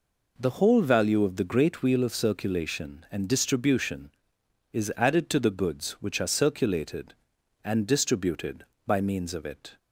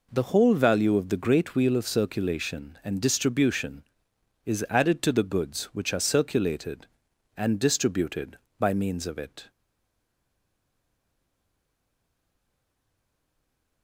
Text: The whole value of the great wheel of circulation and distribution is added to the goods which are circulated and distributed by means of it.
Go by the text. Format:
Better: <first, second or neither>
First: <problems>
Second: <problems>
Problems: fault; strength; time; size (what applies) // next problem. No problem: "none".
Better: first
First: none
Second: stays silent after the last word; strong; from 9.5 s on; 4.3 s long